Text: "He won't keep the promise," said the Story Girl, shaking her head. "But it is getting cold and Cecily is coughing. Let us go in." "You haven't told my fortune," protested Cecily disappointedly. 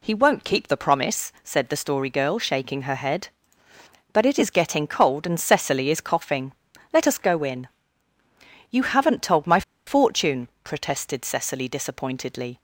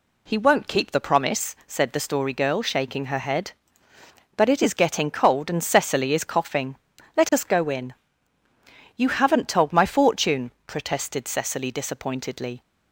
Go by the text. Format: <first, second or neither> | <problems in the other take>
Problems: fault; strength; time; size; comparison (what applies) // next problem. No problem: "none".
second | pauses between "my" and "fortune"; slight; at 9.6 s; 0.25 s long